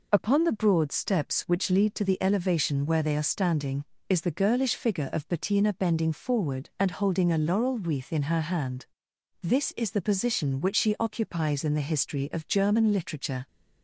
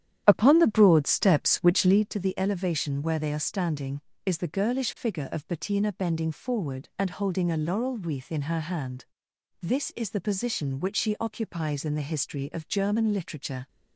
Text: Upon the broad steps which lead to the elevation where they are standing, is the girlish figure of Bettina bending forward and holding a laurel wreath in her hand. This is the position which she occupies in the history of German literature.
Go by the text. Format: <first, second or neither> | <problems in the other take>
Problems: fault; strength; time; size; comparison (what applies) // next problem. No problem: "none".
first | starts louder than the rest; strong; until 2.1 s; 10.5 dB